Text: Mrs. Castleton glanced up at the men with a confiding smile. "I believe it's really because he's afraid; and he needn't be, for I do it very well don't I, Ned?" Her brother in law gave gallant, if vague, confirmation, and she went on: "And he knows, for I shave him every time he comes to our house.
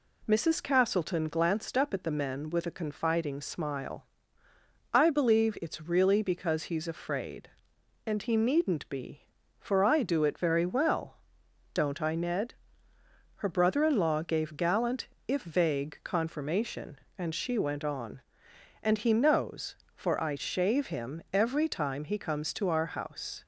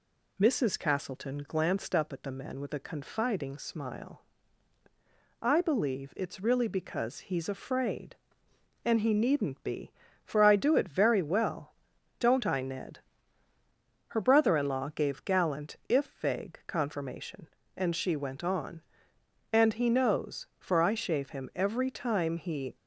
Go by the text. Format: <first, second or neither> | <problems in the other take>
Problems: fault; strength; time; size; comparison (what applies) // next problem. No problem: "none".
first | pauses between "well" and "don't"; noticeable; at 11.7 s; 0.46 s long; noticeable in the first // stops before "comes to our house"; at 22.7 s